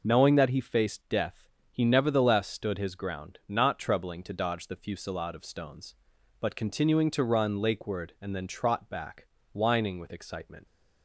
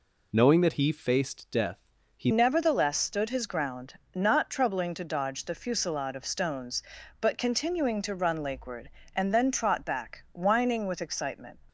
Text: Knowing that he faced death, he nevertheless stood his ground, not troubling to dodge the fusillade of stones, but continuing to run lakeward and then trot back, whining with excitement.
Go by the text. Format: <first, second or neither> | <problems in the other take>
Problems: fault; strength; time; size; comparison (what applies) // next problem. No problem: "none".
first | changes voice at "nevertheless"; from 2.3 s on; 9.2 s long